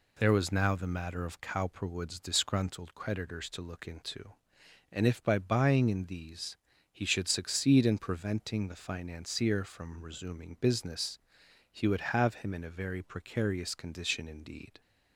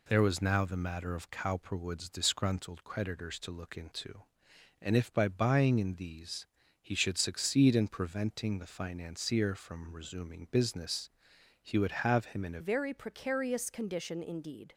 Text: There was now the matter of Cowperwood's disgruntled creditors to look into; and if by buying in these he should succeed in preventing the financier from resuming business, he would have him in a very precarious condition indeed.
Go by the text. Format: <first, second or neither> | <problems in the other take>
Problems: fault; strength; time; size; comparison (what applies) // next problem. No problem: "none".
first | pauses between "these" and "he"; slight; at 6.4 s; 0.36 s long; slight in the first // changes voice at "very"; from 12.6 s on; 2.1 s long